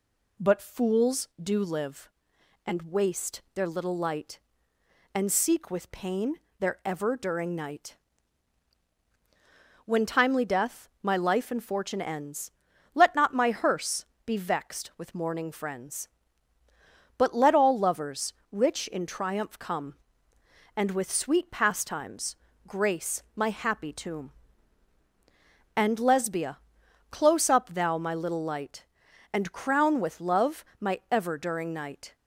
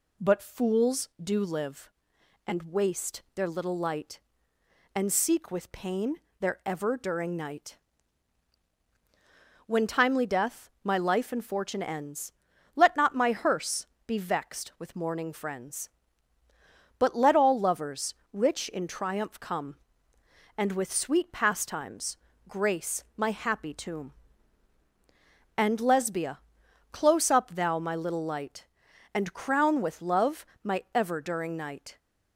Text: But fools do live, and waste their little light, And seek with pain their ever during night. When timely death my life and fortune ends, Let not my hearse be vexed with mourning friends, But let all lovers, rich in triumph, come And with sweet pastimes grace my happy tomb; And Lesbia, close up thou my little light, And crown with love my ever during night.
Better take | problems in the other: neither | pauses between "pain" and "their"; slight; the same in both // pauses between "hearse" and "be"; slight; the same in both // pauses between "pastimes" and "grace"; slight; the same in both // pauses between "love" and "my"; slight; the same in both

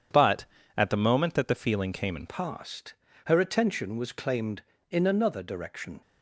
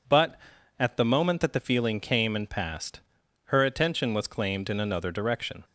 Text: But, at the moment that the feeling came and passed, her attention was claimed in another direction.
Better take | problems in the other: second | changes voice at "passed"; from 2.2 s on; 3.8 s long

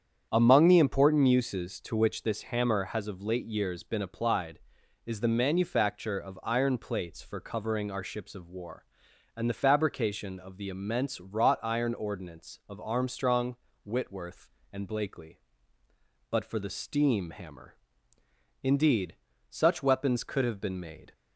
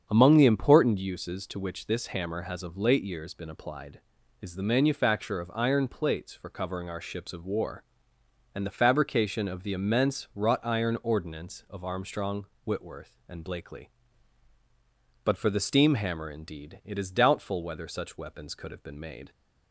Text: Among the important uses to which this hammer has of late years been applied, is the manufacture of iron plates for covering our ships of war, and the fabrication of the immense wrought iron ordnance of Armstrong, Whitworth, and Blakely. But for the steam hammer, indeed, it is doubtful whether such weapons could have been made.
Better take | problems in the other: second | starts louder than the rest; strong; until 1.3 s; 8.5 dB; strong in the second // skips "it is doubtful whether"; at 19.3 s

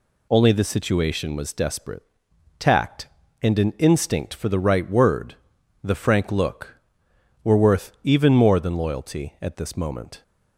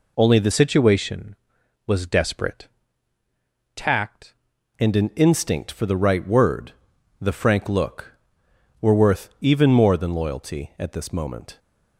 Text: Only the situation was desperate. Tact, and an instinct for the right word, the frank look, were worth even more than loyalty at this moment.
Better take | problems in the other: first | changes voice from "situation" to "Tact"; from 0.5 to 4.3 s; 3.8 s long

